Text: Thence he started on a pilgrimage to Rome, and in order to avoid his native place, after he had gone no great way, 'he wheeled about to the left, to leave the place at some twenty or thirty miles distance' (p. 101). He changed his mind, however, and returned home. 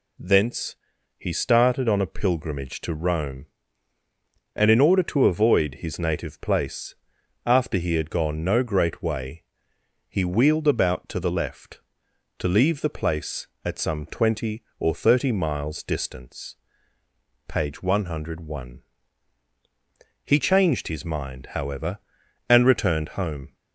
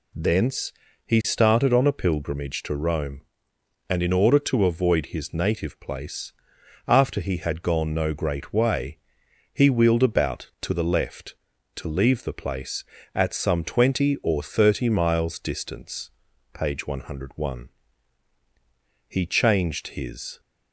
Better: first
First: pauses between "Thence" and "he"; at 0.7 s; 0.42 s long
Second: pauses between "Thence" and "he"; slight; at 0.7 s; 0.32 s long // stops before "mind however and returned home"; at 20.3 s

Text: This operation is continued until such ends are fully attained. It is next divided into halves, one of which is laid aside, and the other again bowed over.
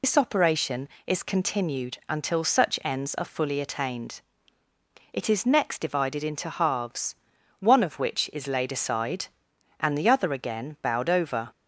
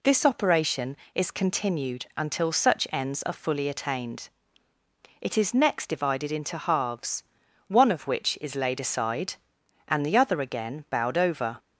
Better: second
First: loses the start of "This"; at 0.0 s; 95 ms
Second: none

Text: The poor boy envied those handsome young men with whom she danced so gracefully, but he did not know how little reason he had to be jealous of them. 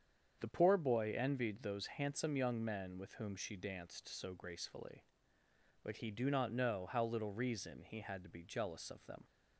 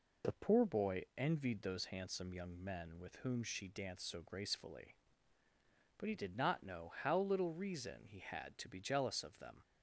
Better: second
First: starts louder than the rest; strong; until 1.4 s; 7.5 dB // says "do" for "did"; at 6.1 s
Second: none

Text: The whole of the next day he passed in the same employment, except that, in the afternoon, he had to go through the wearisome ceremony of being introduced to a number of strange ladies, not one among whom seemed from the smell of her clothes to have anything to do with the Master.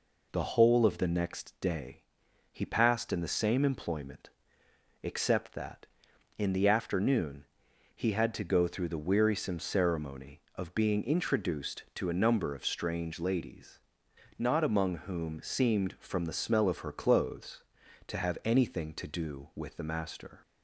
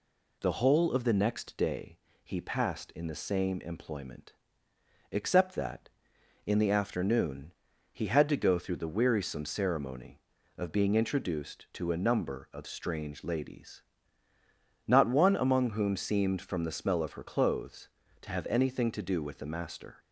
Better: second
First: pauses between "day" and "he"; noticeable; at 2.0 s; 0.50 s long // skips "one"; at 14.6 s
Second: pauses between "day" and "he"; slight; at 1.9 s; 0.24 s long

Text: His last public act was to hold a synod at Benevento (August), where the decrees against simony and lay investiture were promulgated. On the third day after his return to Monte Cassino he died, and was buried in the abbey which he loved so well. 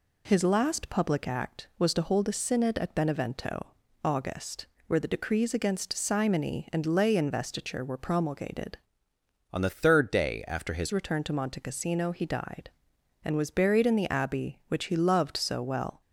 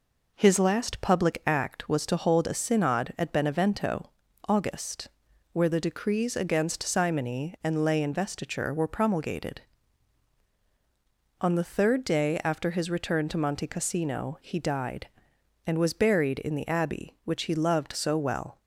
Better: second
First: changes voice from "On" to "his"; from 9.5 to 10.9 s; 1.4 s long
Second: none

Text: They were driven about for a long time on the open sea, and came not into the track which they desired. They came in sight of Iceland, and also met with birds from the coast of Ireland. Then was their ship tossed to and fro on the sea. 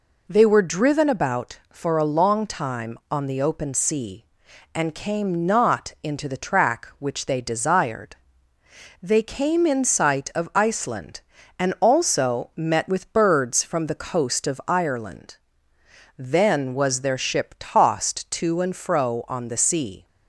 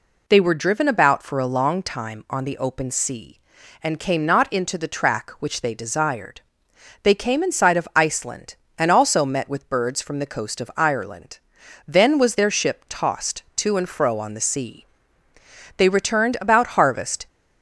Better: first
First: none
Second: goes on to say "They returned about harvest"; from 15.7 s on; 1.5 s long

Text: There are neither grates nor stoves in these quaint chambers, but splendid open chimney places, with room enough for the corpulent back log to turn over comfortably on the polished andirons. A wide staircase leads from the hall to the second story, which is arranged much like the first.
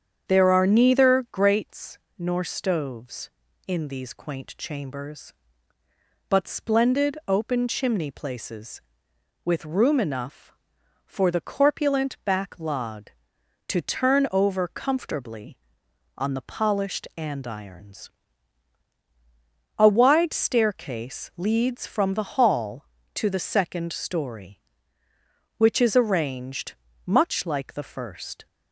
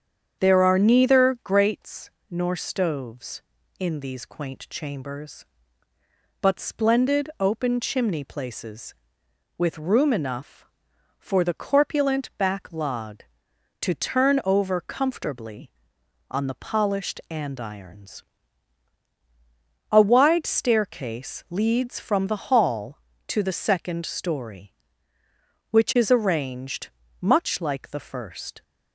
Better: neither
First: starts louder than the rest; strong; until 1.3 s; 8 dB // pauses between "grates" and "nor"; slight; at 1.9 s; 0.20 s long // pauses between "arranged" and "much"; slight; at 26.7 s; 0.32 s long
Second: starts louder than the rest; strong; until 1.4 s; 8 dB // pauses between "grates" and "nor"; slight; at 2.1 s; 0.20 s long // pauses between "arranged" and "much"; slight; at 26.8 s; 0.32 s long

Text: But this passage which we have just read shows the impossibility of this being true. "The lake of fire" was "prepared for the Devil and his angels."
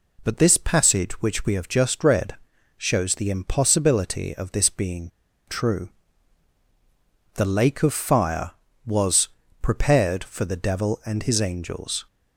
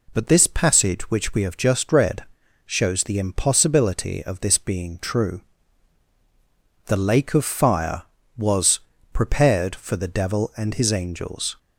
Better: second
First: pauses between "read" and "shows"; at 2.3 s; 0.40 s long // pauses between "being" and "true"; at 5.0 s; 0.38 s long // pauses between "was" and "prepared"; slight; at 9.2 s; 0.32 s long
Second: pauses between "read" and "shows"; at 2.2 s; 0.40 s long // pauses between "was" and "prepared"; slight; at 8.7 s; 0.32 s long

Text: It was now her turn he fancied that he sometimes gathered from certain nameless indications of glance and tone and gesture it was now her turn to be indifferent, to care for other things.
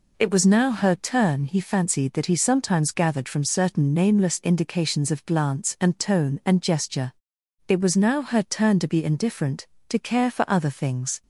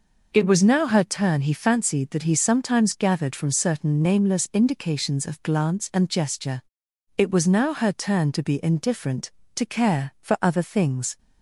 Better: first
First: pauses between "gesture" and "it"; noticeable; at 7.1 s; 0.54 s long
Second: skips "tone and"; at 6.0 s // pauses between "gesture" and "it"; noticeable; at 6.6 s; 0.56 s long

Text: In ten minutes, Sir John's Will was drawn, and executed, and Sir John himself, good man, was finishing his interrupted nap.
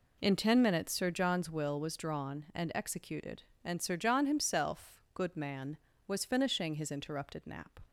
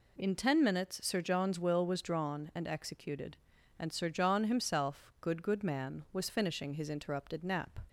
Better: first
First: none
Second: says "good" twice; at 5.4 s

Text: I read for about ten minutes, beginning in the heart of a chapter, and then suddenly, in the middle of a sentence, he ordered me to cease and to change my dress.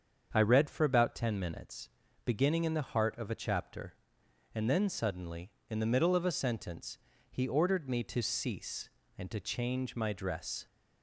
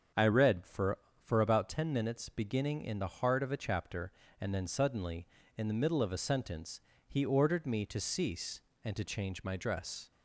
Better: first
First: starts louder than the rest; until 1.3 s; 7 dB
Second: starts louder than the rest; strong; until 1.4 s; 7.5 dB // says "for" twice; at 1.2 s

